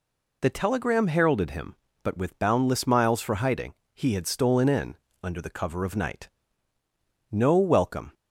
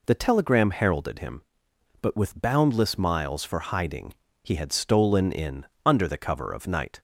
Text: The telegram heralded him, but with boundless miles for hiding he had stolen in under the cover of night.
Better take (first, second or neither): second